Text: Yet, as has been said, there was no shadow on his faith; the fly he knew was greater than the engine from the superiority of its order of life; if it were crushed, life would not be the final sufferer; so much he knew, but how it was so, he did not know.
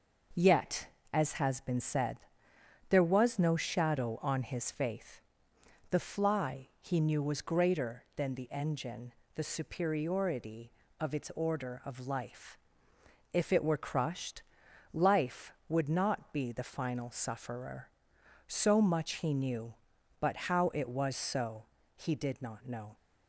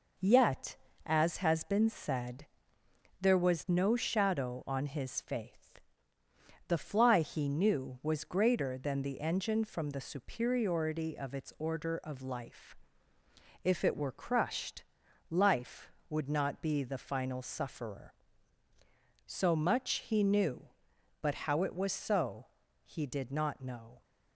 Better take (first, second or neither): second